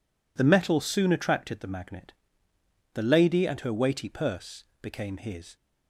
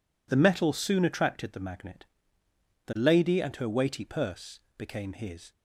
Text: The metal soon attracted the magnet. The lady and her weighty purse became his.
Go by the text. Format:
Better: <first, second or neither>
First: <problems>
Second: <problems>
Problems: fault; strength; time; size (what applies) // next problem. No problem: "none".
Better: neither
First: pauses between "purse" and "became"; slight; at 4.6 s; 0.16 s long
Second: pauses between "purse" and "became"; slight; at 4.6 s; 0.16 s long